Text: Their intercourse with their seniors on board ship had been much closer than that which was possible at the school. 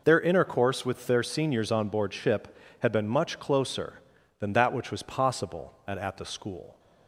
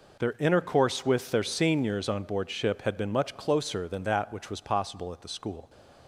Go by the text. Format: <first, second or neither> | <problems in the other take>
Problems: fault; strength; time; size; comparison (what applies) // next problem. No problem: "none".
second | says "at" twice; at 5.9 s